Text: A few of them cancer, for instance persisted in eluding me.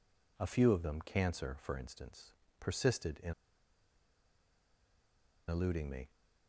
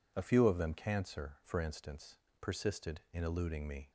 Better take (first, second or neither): second